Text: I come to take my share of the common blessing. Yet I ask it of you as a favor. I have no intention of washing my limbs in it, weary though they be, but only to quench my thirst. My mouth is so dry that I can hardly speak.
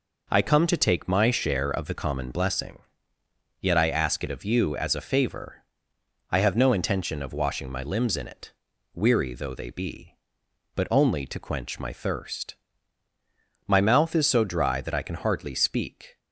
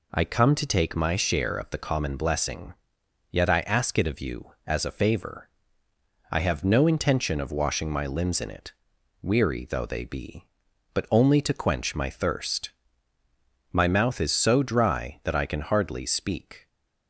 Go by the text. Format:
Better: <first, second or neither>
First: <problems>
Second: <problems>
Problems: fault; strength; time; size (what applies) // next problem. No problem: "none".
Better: neither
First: none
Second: none